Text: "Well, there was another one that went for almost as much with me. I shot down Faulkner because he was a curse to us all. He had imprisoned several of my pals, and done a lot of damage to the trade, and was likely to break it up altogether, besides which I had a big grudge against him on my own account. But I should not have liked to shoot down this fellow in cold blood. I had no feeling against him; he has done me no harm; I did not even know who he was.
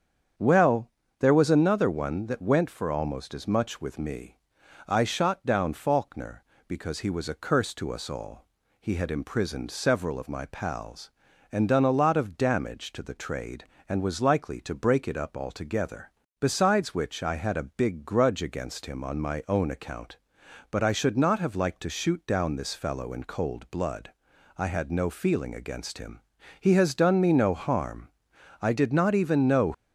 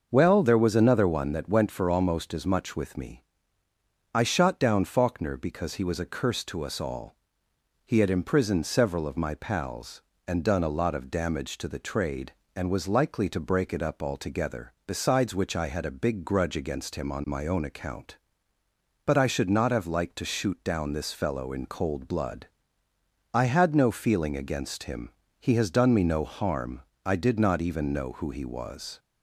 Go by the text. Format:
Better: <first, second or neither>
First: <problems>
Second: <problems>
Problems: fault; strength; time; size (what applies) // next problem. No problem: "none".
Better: second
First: starts louder than the rest; strong; until 1.6 s; 8 dB // stops before "who he was"; at 29.7 s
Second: starts louder than the rest; noticeable; until 1.1 s; 6 dB